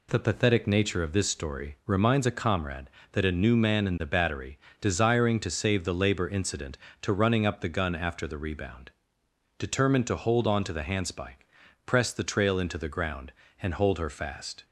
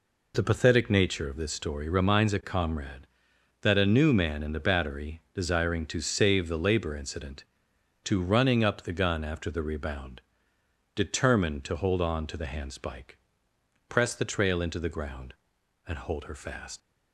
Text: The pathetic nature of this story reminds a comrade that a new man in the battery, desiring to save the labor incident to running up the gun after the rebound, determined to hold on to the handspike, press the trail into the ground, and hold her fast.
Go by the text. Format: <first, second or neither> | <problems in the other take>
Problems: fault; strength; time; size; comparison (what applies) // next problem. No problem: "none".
first | leaves "fast" unfinished; at 16.8 s; 70 ms